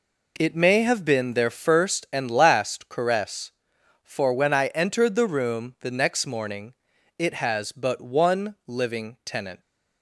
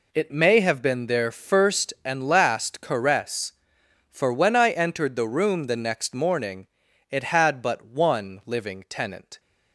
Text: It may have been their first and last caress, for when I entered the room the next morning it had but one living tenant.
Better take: second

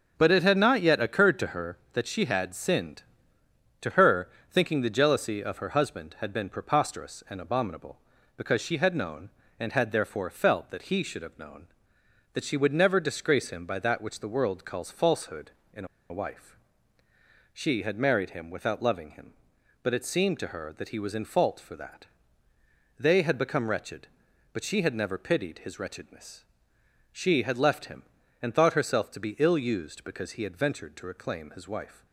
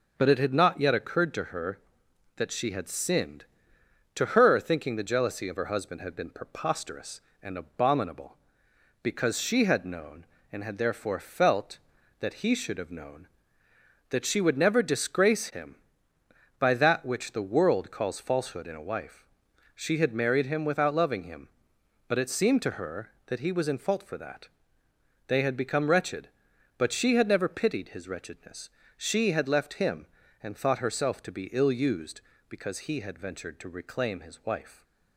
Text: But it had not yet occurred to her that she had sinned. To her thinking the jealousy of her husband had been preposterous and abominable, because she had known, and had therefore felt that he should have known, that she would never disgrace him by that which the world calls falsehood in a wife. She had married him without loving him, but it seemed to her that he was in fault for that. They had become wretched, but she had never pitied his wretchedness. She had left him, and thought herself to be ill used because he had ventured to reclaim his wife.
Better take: second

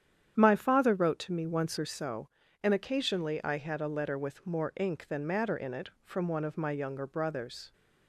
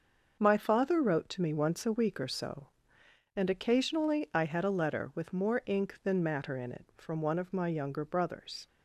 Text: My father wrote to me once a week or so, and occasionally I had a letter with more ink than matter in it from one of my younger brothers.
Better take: second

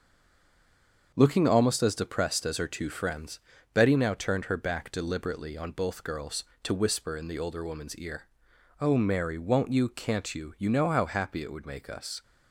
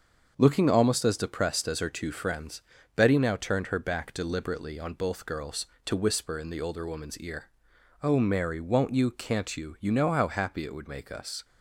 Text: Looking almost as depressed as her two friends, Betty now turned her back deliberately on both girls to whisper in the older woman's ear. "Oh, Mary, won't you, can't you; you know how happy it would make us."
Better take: second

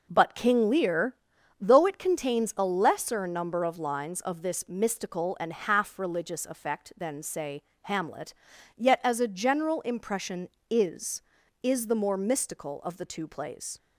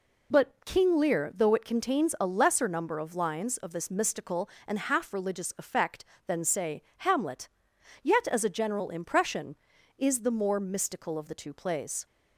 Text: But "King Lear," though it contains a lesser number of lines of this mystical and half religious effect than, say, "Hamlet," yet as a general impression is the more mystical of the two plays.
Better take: second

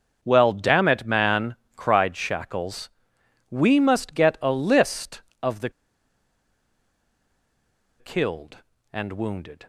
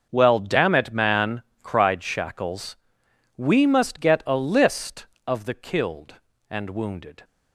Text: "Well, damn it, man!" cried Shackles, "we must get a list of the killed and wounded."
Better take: second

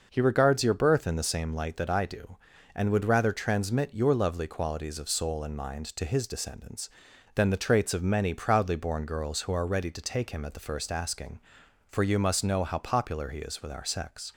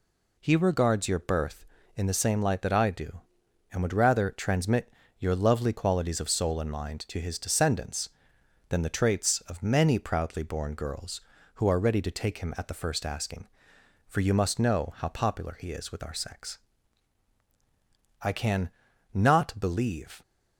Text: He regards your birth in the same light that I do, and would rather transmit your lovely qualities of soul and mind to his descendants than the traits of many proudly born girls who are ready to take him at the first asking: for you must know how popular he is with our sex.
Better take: first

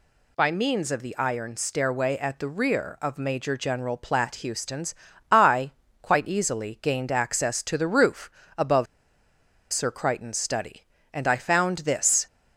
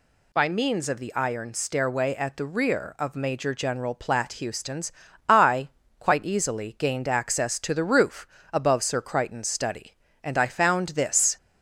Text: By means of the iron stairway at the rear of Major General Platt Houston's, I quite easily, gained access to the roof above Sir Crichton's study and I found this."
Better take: second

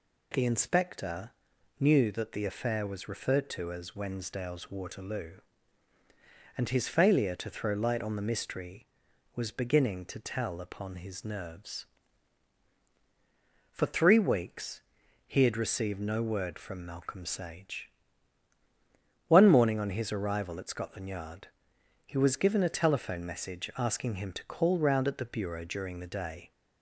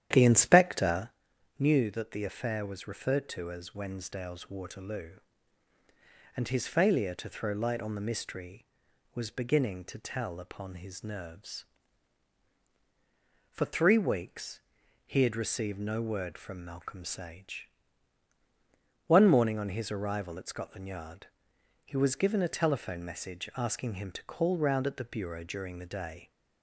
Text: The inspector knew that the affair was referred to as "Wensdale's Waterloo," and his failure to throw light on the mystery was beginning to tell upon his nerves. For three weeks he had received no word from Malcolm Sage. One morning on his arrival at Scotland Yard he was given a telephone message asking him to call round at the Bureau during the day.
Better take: first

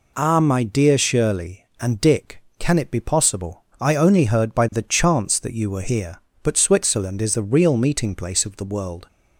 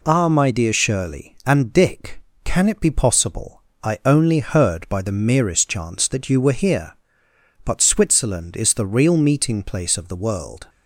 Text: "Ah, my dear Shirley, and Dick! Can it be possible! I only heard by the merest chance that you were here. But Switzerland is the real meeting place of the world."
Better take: second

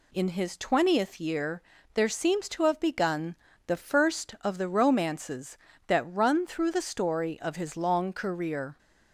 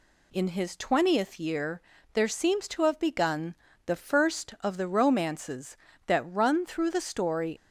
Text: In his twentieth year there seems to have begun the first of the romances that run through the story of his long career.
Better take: first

